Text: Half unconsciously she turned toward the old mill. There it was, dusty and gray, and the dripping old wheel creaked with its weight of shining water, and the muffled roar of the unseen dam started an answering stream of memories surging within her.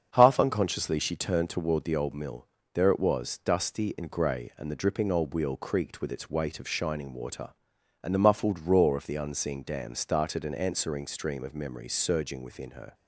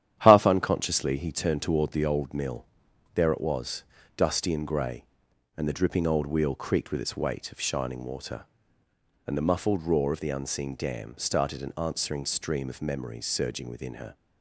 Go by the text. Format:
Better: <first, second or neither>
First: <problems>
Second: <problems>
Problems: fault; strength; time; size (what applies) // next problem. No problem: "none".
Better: first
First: starts louder than the rest; strong; until 1.1 s; 7 dB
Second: starts louder than the rest; strong; until 1.2 s; 10.5 dB // says "he" for "she"; at 1.1 s